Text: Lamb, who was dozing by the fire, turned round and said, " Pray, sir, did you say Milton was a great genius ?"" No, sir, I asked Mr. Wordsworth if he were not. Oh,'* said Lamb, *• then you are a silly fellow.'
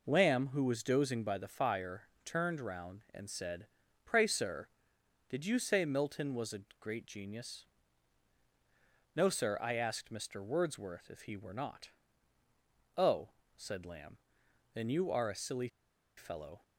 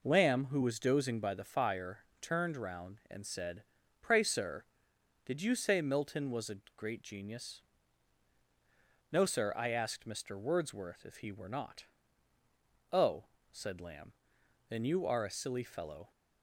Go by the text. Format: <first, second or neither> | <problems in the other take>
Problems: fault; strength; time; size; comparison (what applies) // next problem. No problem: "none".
second | pauses between "a" and "great"; slight; at 6.6 s; 0.18 s long; slight in the second // pauses between "silly" and "fellow"; noticeable; at 15.6 s; 0.48 s long